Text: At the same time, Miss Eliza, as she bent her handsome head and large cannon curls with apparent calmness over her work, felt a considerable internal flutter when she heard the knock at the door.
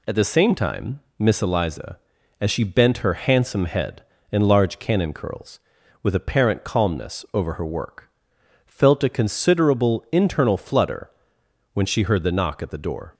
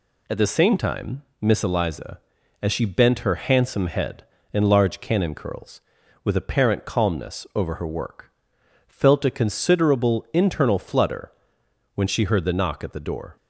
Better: neither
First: pauses between "flutter" and "when"; noticeable; at 11.1 s; 0.64 s long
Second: pauses between "flutter" and "when"; noticeable; at 11.3 s; 0.64 s long

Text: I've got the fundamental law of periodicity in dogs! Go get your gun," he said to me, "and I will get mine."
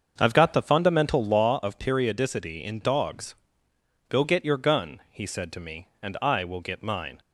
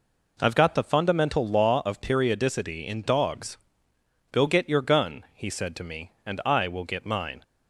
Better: second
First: starts louder than the rest; until 1.5 s; 6.5 dB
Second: none

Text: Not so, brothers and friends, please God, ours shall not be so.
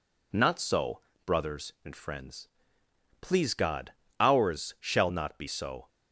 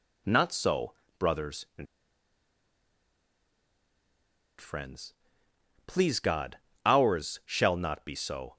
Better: first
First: none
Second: pauses between "and" and "friends"; strong; at 1.8 s; 2.7 s long

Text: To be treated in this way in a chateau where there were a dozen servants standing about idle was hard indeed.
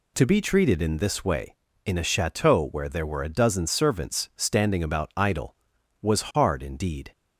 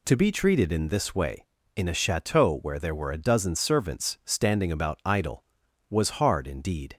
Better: neither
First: none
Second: none

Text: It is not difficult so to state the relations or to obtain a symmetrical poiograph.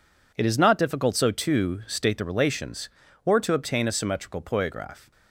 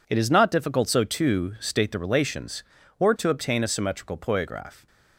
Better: neither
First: none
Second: none

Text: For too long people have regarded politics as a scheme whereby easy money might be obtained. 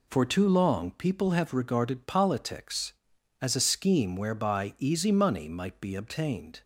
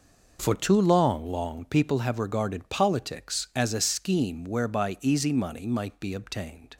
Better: first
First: none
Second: says "long" twice; at 1.3 s

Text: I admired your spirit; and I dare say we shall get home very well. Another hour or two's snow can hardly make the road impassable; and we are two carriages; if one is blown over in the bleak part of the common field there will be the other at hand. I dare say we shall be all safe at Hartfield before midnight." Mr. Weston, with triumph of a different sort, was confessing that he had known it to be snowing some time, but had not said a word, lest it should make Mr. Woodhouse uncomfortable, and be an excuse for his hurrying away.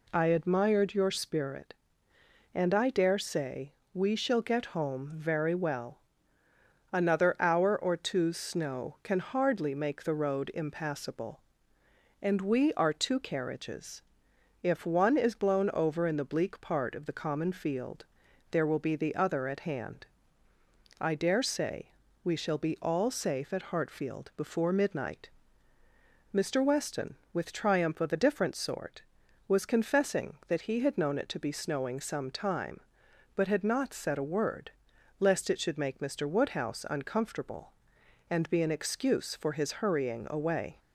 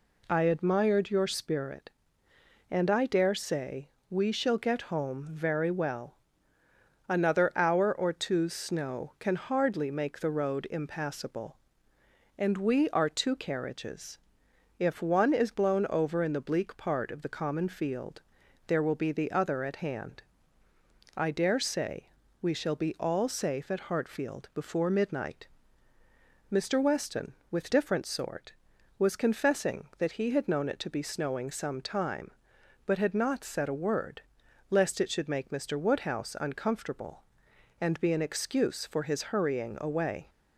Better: first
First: pauses between "say" and "we"; slight; at 3.7 s; 0.20 s long // pauses between "field" and "there"; at 18.0 s; 0.44 s long // pauses between "say" and "we"; slight; at 21.8 s; 0.34 s long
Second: pauses between "say" and "we"; slight; at 3.8 s; 0.20 s long // pauses between "field" and "there"; at 18.2 s; 0.44 s long // pauses between "say" and "we"; slight; at 22.0 s; 0.34 s long // skips "triumph of a"; at 27.6 s

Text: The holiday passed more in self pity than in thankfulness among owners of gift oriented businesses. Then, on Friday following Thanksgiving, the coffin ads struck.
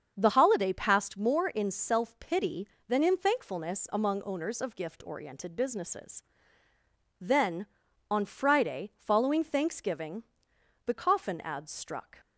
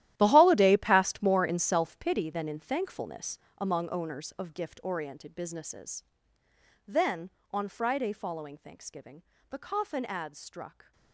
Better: first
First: starts louder than the rest; until 1.1 s; 7 dB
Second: gets quieter; strong; throughout; 16 dB // starts louder than the rest; strong; until 1.1 s; 13 dB // pauses between "thankfulness" and "among"; slight; at 3.3 s; 0.20 s long

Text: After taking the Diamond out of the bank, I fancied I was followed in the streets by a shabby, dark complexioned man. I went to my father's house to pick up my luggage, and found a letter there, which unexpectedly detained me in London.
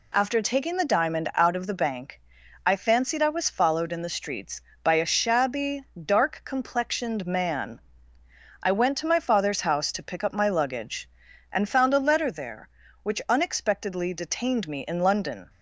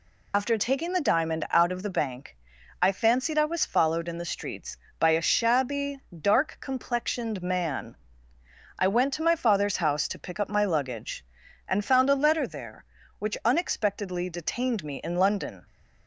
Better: first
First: none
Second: loses the start of "After"; at 0.3 s; 60 ms

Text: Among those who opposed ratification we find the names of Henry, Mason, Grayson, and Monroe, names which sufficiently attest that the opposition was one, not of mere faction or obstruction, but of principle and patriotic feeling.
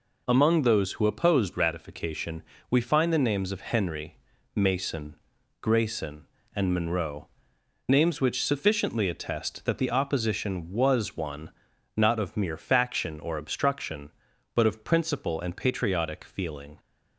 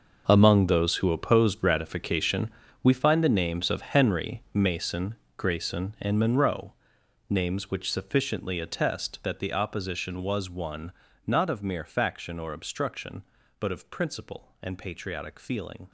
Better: first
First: pauses between "ratification" and "we"; slight; at 2.4 s; 0.26 s long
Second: gets quieter; strong; throughout; 14 dB // pauses between "ratification" and "we"; slight; at 2.5 s; 0.32 s long

